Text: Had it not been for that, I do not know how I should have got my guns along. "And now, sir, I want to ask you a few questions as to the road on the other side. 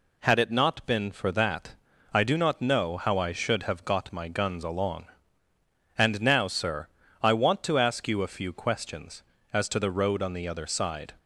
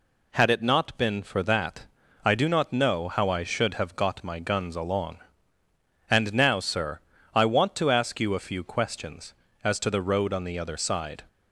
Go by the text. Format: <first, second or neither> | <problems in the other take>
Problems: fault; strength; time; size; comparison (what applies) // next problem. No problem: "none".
neither | none